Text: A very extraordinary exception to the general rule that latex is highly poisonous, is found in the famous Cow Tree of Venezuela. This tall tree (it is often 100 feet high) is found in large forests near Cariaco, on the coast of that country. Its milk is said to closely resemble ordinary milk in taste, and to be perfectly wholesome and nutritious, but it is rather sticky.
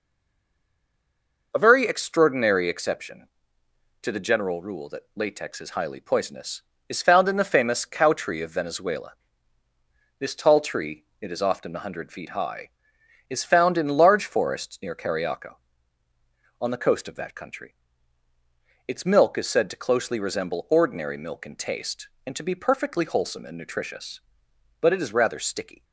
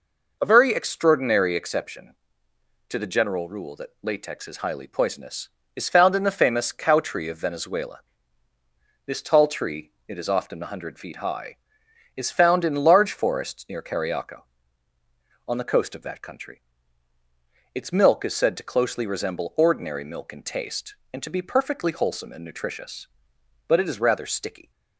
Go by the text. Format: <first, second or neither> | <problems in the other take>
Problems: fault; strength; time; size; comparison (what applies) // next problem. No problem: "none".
second | stays silent before the first word; noticeable; until 1.5 s; 1.5 s long